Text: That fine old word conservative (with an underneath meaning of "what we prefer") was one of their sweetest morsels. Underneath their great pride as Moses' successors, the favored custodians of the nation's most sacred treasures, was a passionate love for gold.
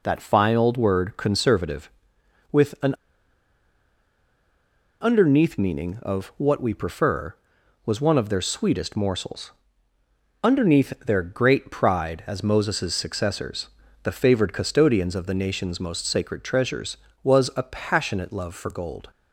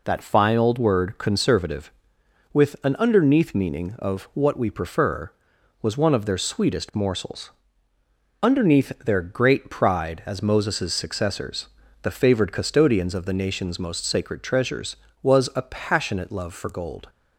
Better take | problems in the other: second | pauses between "an" and "underneath"; strong; at 2.9 s; 2.0 s long

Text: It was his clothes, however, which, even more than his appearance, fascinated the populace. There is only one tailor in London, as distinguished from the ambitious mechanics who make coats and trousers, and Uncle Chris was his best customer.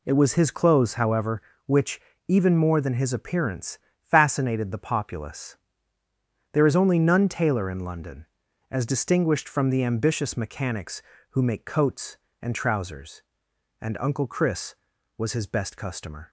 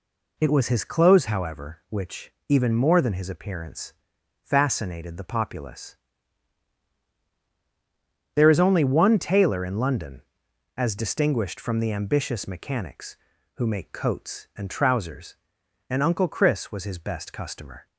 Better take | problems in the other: second | says "none" for "one"; at 6.9 s

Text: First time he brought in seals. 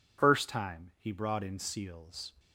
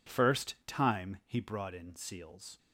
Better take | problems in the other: neither | none

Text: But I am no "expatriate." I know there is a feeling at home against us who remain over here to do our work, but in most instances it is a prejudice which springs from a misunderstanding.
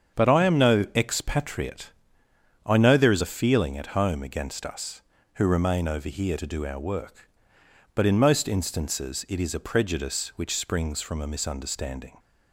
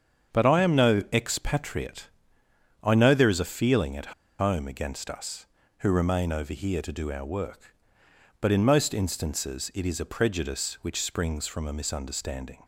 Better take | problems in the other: first | starts louder than the rest; strong; until 1.4 s; 7.5 dB; strong in the first // pauses between "at" and "home"; slight; at 4.1 s; 0.28 s long

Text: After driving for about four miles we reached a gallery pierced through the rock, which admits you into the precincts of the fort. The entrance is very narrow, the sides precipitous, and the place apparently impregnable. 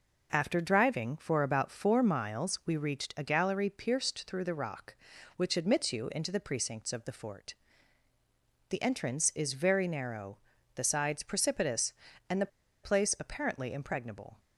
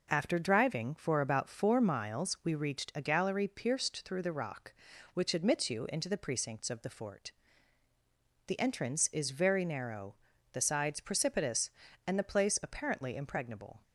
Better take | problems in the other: second | pauses between "the" and "place"; slight; at 12.4 s; 0.34 s long

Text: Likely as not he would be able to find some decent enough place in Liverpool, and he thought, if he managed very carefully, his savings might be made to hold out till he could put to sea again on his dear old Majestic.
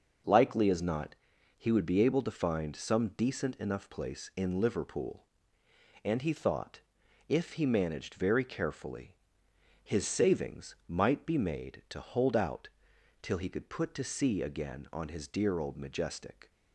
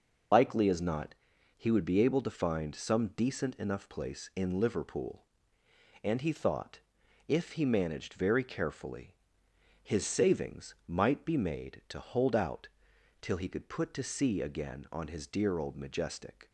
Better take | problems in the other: first | loses the start of "Likely"; at 0.3 s; 65 ms // starts louder than the rest; noticeable; until 1.7 s; 6 dB; noticeable in the first // pauses between "not" and "he"; at 1.1 s; 0.44 s long; also in the first // pauses between "out" and "till"; noticeable; at 12.6 s; 0.54 s long; noticeable in the first

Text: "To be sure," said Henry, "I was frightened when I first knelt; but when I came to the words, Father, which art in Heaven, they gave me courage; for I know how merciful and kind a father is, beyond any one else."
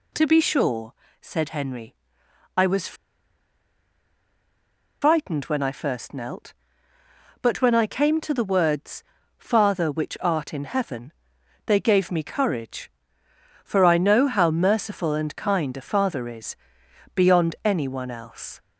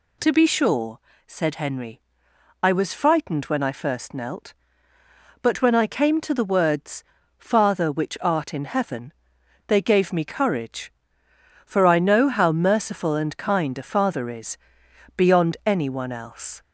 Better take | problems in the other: second | pauses between "was" and "frightened"; strong; at 2.9 s; 2.0 s long

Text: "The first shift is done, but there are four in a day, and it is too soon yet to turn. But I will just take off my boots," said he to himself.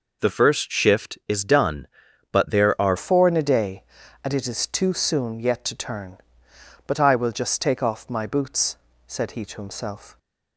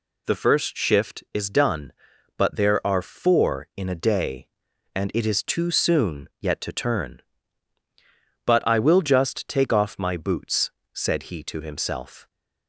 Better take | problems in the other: second | changes voice at "four"; from 2.9 s on; 7.2 s long

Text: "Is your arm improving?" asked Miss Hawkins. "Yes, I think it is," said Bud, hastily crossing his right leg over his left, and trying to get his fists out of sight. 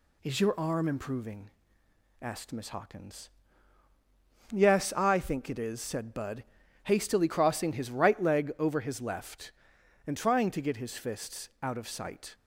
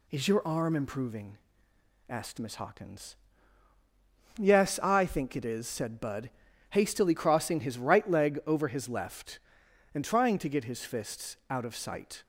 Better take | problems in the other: neither | none

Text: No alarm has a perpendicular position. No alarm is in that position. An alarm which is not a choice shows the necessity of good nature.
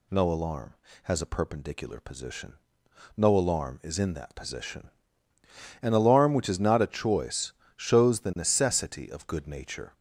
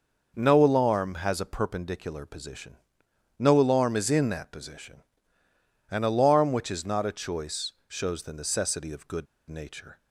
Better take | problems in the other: first | pauses between "choice" and "shows"; slight; at 7.7 s; 0.16 s long; slight in the first // pauses between "good" and "nature"; slight; at 9.2 s; 0.23 s long

